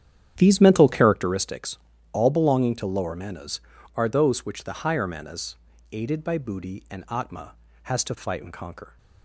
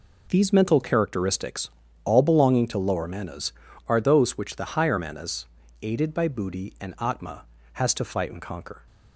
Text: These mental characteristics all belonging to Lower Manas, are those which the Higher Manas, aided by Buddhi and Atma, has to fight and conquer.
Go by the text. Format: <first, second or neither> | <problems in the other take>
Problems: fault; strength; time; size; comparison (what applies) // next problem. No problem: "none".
second | starts louder than the rest; strong; until 1.4 s; 10 dB // pauses between "characteristics" and "all"; slight; at 1.7 s; 0.34 s long; slight in the second